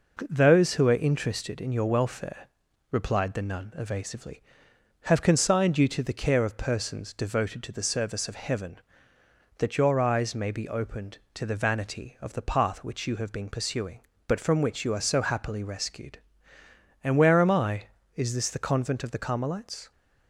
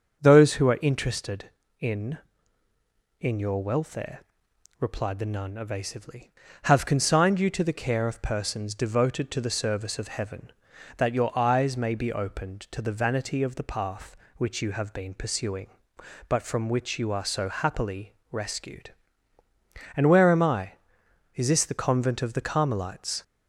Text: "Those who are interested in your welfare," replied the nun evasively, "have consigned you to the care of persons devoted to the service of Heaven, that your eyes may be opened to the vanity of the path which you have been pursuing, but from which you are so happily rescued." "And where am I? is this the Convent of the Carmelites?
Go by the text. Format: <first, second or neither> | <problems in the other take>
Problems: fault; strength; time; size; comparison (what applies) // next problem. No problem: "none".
first | starts louder than the rest; until 1.2 s; 7 dB // says "in" twice; at 3.2 s // pauses between "happily" and "rescued"; slight; at 18.1 s; 0.16 s long